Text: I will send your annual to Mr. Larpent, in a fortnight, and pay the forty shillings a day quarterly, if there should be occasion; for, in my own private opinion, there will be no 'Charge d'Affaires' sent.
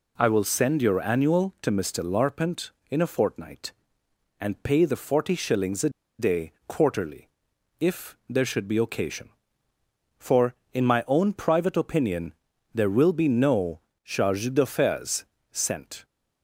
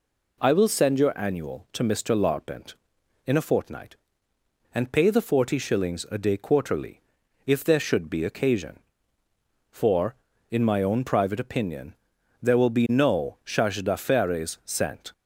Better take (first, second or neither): second